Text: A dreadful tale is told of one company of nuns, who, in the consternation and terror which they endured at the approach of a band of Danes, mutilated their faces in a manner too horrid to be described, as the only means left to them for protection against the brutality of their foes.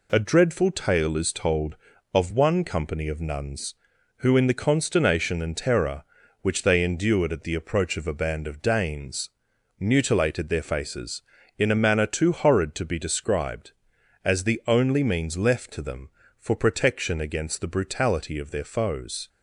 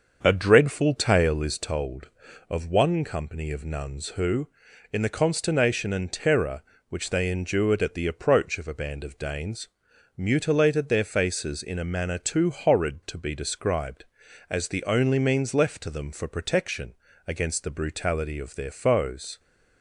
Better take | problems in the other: first | starts louder than the rest; until 1.7 s; 6.5 dB // pauses between "protection" and "against"; slight; at 16.9 s; 0.34 s long

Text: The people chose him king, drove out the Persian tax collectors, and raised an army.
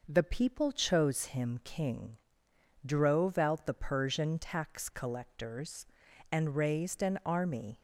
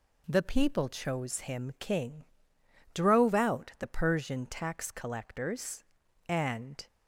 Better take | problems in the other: first | stops before "raised an army"; at 6.8 s

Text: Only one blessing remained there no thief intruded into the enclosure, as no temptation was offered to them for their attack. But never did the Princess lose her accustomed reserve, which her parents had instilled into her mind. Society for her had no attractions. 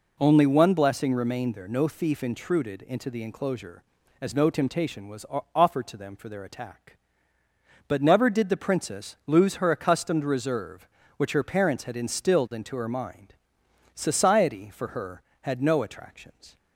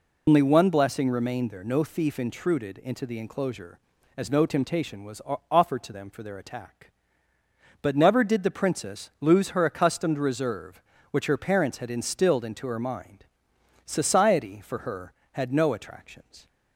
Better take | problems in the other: first | loses the start of "Only"; at 0.2 s; 120 ms // pauses between "was" and "offered"; slight; at 5.2 s; 0.28 s long; slight in the first

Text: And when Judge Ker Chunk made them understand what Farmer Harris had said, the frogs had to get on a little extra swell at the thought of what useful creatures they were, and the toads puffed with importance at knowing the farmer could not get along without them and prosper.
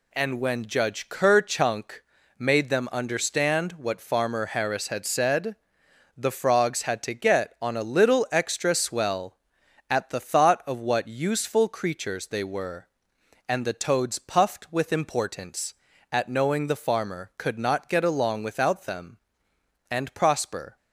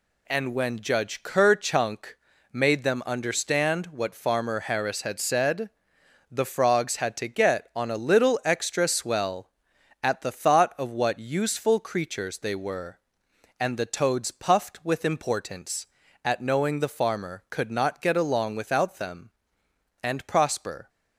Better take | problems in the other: neither | pauses between "Chunk" and "made"; slight; the same in both

